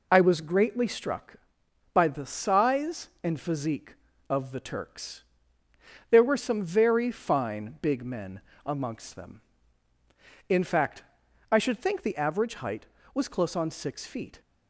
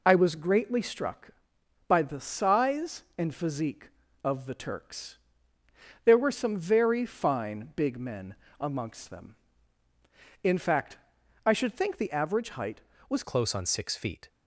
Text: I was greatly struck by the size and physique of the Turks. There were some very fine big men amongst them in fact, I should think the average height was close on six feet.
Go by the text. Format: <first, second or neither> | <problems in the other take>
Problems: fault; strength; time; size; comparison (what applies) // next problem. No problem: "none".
first | pauses between "men" and "amongst"; slight; at 8.3 s; 0.24 s long; slight in the first // changes voice at "close"; from 13.2 s on; 1.0 s long